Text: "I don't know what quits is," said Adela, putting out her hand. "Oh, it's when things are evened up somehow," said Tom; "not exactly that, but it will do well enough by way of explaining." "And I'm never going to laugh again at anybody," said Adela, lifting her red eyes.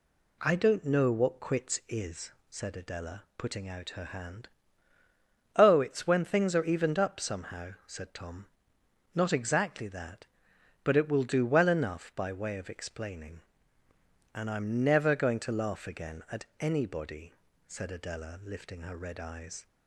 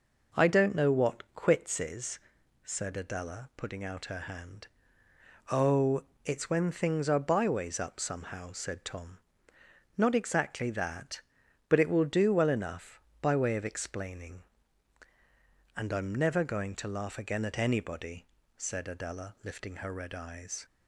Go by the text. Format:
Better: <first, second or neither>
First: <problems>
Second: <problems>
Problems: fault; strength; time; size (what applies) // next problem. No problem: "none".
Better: first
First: none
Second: says "byways" for "evened"; at 7.1 s